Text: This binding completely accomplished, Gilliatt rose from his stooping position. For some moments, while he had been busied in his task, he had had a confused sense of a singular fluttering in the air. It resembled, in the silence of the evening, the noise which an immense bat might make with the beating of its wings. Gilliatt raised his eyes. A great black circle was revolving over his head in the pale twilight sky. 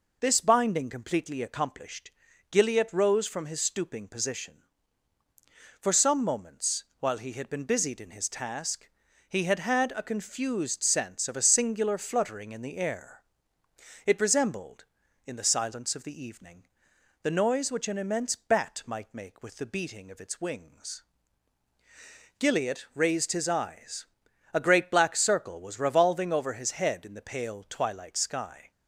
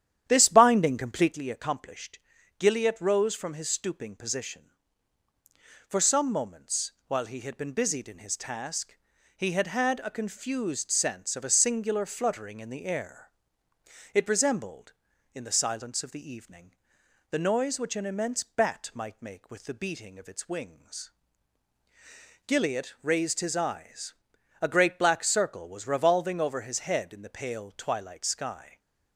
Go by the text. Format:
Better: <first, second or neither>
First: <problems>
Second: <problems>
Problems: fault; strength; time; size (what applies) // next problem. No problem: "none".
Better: first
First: none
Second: starts louder than the rest; strong; until 1.4 s; 10.5 dB // stays silent after the last word; slight; from 28.6 s on; 0.5 s long